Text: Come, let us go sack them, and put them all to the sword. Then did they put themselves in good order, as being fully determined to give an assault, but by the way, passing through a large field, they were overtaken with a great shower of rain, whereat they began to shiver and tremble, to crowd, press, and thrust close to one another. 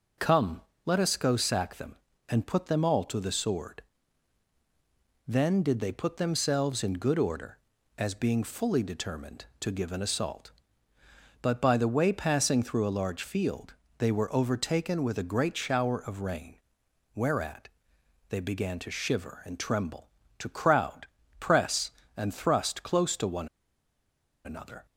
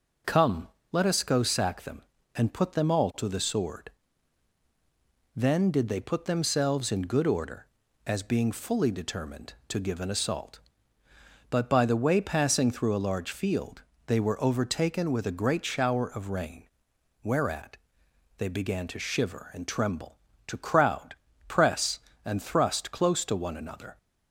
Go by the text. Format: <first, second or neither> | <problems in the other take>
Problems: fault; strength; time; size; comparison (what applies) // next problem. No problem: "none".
second | pauses between "whereat" and "they"; noticeable; at 17.6 s; 0.60 s long; noticeable in the second // pauses between "one" and "another"; noticeable; at 23.4 s; 0.97 s long